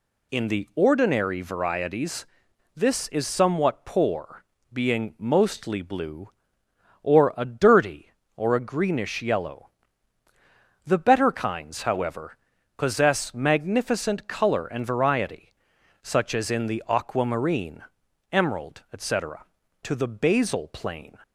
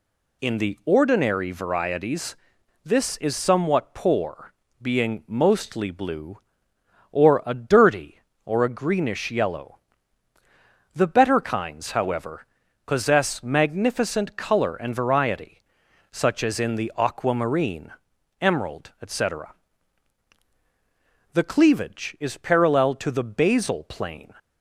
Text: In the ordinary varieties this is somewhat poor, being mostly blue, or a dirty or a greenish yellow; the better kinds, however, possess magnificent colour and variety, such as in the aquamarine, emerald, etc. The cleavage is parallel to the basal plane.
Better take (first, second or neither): second